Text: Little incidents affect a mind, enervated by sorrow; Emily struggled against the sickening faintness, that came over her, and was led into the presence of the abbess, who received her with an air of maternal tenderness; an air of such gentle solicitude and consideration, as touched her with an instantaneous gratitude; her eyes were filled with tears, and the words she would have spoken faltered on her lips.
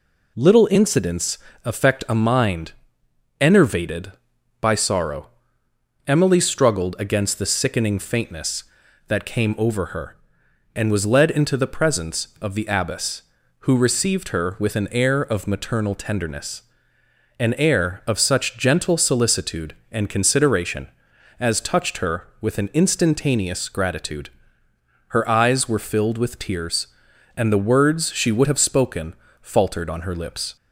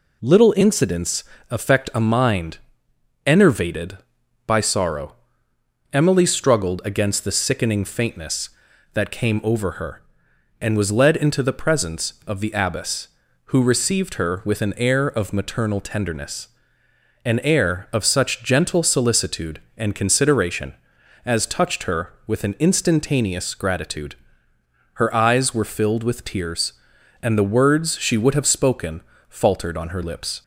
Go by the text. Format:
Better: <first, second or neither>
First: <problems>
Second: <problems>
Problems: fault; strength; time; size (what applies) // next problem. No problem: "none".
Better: neither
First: pauses between "incidents" and "affect"; slight; at 1.3 s; 0.28 s long // pauses between "spoken" and "faltered"; slight; at 29.1 s; 0.26 s long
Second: pauses between "incidents" and "affect"; slight; at 1.2 s; 0.28 s long // pauses between "spoken" and "faltered"; slight; at 29.0 s; 0.26 s long